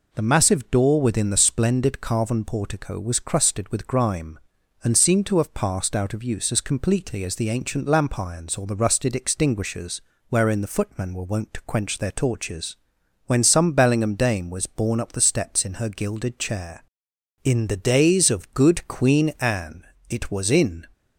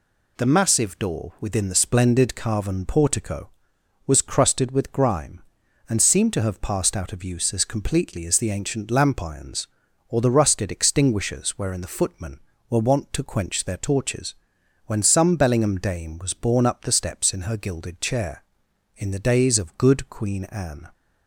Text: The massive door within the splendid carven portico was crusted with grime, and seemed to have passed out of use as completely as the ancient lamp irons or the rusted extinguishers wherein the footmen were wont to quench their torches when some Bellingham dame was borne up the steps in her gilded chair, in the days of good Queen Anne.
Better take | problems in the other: second | pauses between "extinguishers" and "wherein"; slight; at 10.0 s; 0.26 s long // pauses between "torches" and "when"; noticeable; at 12.7 s; 0.52 s long; noticeable in the second // goes on to say "It was in"; noticeable; from 20.0 s on; 0.76 s long

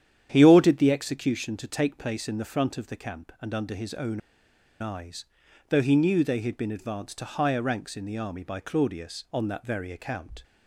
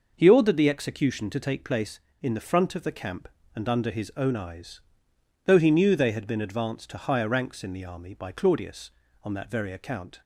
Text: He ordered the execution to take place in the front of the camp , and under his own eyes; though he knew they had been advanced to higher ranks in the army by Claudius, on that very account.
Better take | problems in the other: second | starts louder than the rest; strong; until 1.3 s; 9.5 dB // pauses between "own" and "eyes"; noticeable; at 4.2 s; 0.60 s long

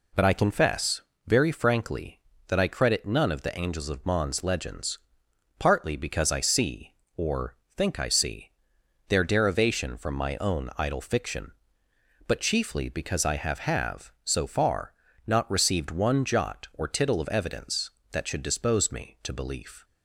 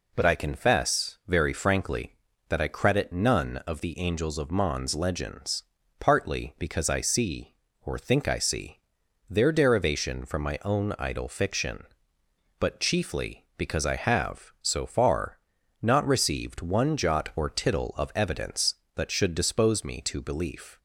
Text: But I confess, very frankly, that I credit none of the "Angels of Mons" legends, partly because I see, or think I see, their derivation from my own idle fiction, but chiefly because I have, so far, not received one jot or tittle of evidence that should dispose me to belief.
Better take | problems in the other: second | pauses between "or" and "think"; slight; at 7.5 s; 0.20 s long // says "have" twice; at 13.5 s

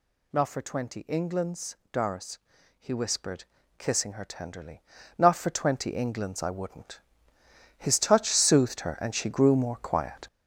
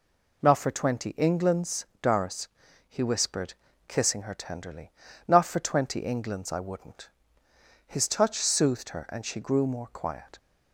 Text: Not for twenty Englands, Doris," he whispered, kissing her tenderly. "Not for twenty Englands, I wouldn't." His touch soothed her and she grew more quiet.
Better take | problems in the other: second | gets louder; noticeable; throughout; 6 dB

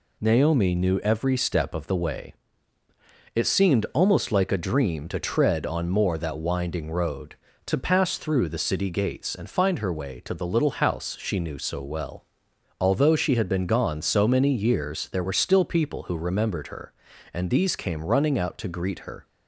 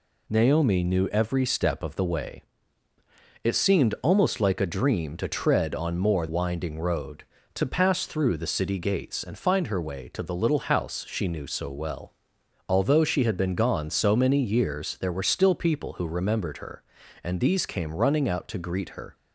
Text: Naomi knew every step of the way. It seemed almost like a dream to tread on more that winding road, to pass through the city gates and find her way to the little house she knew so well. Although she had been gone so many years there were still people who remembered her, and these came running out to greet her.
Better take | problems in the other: first | skips "that"; at 6.2 s

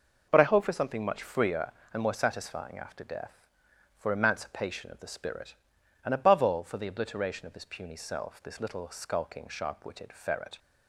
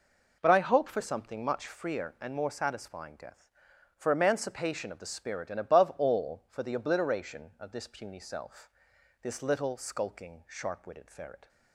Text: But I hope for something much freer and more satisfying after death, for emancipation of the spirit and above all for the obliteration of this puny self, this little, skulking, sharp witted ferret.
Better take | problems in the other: first | skips "after"; at 3.1 s

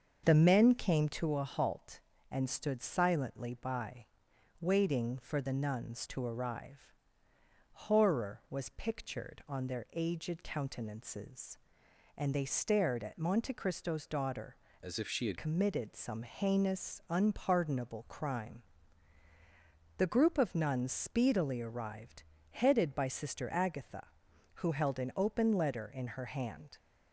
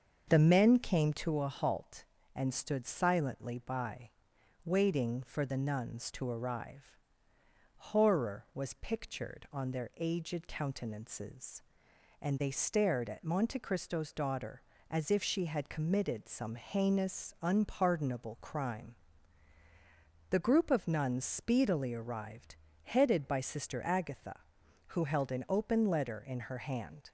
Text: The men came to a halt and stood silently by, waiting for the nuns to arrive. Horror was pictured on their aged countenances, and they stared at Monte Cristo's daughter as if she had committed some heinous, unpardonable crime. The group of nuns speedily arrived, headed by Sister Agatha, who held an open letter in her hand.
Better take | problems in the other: second | starts louder than the rest; until 1.2 s; 6.5 dB; also in the second // changes voice from "as" to "had"; from 14.8 to 15.3 s; 0.5 s long

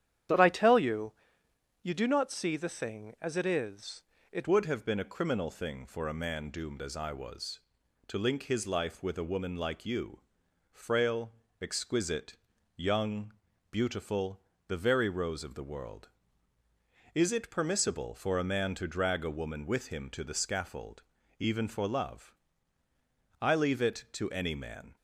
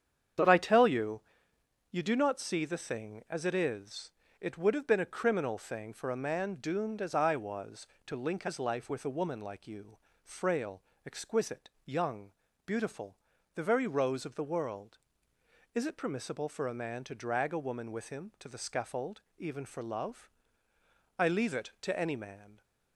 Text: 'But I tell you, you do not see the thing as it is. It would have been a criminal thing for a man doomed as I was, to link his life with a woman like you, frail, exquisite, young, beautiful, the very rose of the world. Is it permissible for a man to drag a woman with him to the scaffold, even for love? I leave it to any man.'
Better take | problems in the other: second | starts louder than the rest; strong; until 2.0 s; 10 dB; strong in the second // changes voice at "would"; from 4.4 s on; 20.5 s long

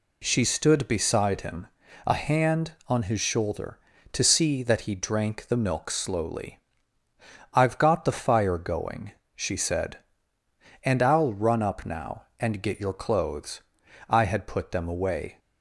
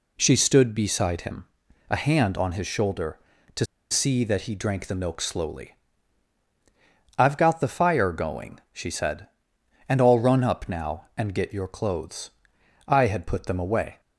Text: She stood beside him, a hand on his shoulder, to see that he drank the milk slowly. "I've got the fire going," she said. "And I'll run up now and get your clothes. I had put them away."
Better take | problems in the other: first | pauses between "to" and "see"; slight; at 3.6 s; 0.25 s long

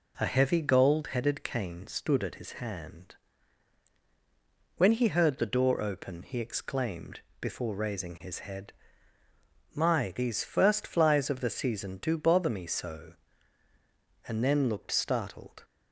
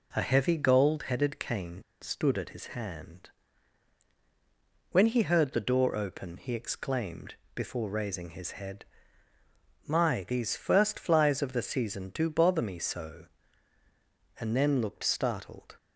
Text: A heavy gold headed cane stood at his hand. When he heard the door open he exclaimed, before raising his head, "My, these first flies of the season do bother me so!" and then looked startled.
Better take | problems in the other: first | pauses between "cane" and "stood"; slight; at 1.8 s; 0.19 s long

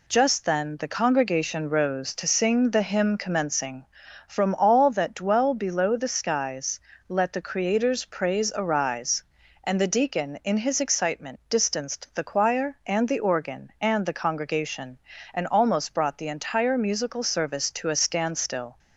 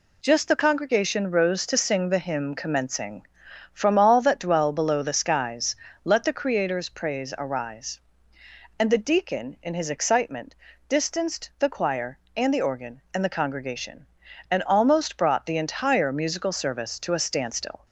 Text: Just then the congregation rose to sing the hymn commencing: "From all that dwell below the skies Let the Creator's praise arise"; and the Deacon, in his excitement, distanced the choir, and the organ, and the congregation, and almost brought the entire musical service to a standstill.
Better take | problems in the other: first | skips "then"; at 0.4 s // pauses between "skies" and "Let"; slight; at 5.7 s; 0.28 s long; slight in the first

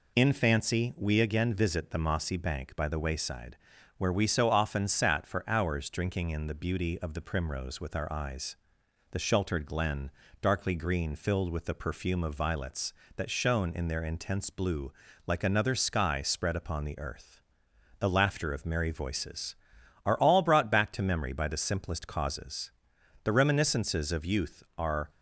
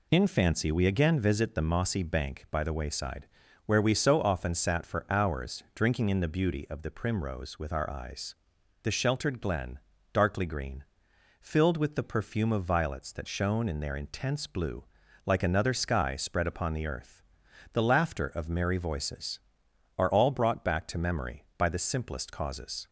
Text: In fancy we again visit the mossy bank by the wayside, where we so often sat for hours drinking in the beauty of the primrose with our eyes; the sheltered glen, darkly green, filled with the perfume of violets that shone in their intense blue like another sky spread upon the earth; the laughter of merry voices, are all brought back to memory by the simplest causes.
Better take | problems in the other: second | pauses between "blue" and "like"; slight; at 14.9 s; 0.32 s long; also in the second // goes on to say "The reminiscences of youth are"; strong; from 23.2 s on; 1.8 s long

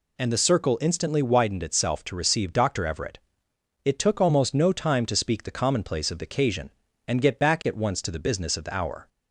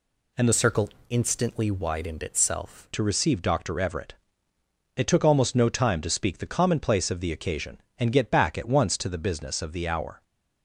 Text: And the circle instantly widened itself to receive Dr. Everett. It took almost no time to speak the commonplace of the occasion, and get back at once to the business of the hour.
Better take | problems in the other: first | changes voice from "circle" to "itself"; from 0.5 to 2.8 s; 2.3 s long // pauses between "circle" and "instantly"; slight; at 0.8 s; 0.20 s long

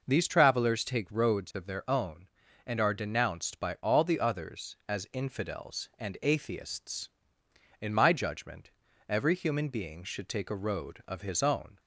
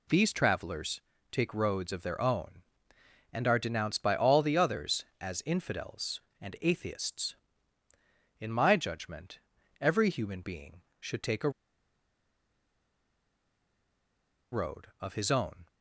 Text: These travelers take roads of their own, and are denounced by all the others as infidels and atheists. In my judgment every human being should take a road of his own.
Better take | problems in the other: first | pauses between "travelers" and "take"; slight; at 1.0 s; 0.30 s long // pauses between "judgment" and "every"; at 9.3 s; 0.40 s long; also in the first // pauses between "a" and "road"; strong; at 11.4 s; 3.0 s long

